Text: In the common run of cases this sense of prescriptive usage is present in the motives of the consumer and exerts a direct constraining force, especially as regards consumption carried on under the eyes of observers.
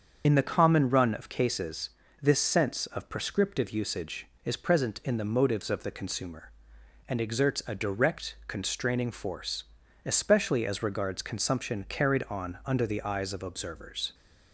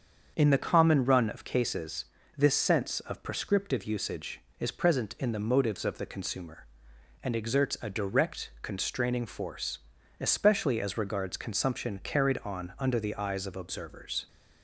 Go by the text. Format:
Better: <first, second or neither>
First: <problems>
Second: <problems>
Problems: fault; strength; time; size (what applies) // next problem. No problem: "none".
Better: second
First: loses the start of "In"; at 0.2 s; 40 ms // starts louder than the rest; until 1.2 s; 7 dB // pauses between "cases" and "this"; slight; at 1.9 s; 0.30 s long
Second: starts louder than the rest; until 1.3 s; 7 dB // pauses between "cases" and "this"; slight; at 2.0 s; 0.30 s long